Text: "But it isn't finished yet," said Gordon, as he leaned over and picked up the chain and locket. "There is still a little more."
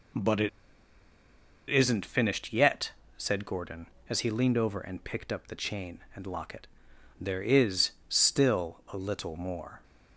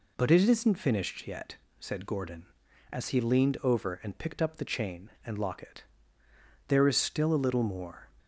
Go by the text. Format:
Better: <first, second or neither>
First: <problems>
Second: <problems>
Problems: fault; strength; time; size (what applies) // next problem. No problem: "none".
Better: second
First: pauses between "it" and "isn't"; at 0.4 s; 1.2 s long // pauses between "is" and "still"; slight; at 7.9 s; 0.18 s long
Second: none